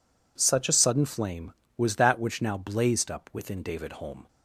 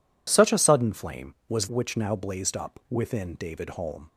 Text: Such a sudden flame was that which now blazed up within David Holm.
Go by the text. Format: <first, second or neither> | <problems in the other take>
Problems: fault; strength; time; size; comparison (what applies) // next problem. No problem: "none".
first | skips "that"; at 1.6 s